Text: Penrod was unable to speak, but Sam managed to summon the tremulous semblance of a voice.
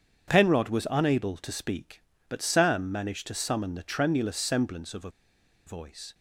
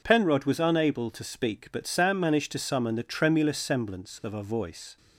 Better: second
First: pauses between "a" and "voice"; noticeable; at 5.0 s; 0.57 s long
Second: none

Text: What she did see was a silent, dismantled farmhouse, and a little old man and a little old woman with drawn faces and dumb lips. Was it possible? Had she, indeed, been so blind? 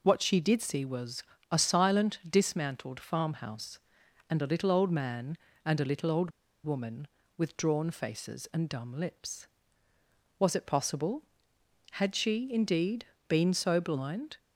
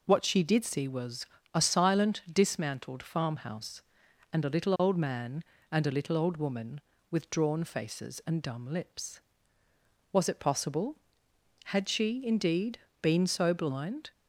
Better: second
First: pauses between "was" and "a"; slight; at 1.2 s; 0.28 s long // pauses between "old" and "woman"; slight; at 6.3 s; 0.33 s long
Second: pauses between "was" and "a"; slight; at 1.2 s; 0.28 s long

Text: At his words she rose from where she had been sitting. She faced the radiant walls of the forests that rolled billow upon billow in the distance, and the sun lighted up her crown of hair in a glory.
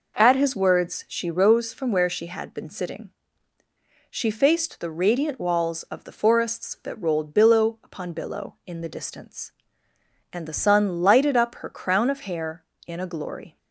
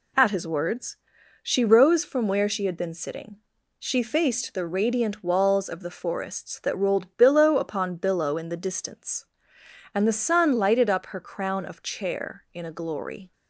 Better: first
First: none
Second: pauses between "words" and "she"; noticeable; at 0.9 s; 0.46 s long // says "chair" for "hair"; at 11.8 s

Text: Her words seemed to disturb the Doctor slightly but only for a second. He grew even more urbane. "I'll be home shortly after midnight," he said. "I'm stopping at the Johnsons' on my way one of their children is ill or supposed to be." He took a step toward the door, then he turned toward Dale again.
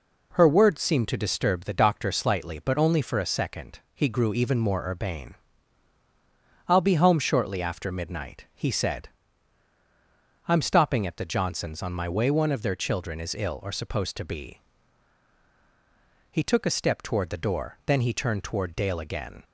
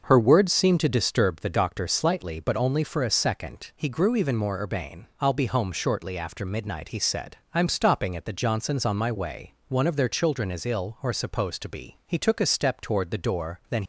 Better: first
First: none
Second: starts louder than the rest; until 1.0 s; 6.5 dB // stops before "he turned toward Dale again"; at 13.8 s

